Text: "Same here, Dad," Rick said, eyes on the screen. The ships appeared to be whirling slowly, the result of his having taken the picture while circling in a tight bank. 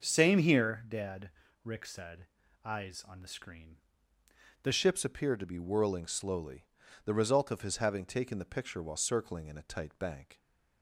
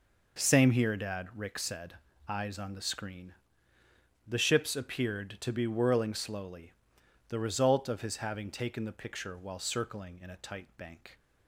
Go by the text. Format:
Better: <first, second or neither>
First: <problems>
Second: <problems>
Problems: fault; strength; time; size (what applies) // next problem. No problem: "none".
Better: second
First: changes voice at "ships"; from 4.7 s on; 5.6 s long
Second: none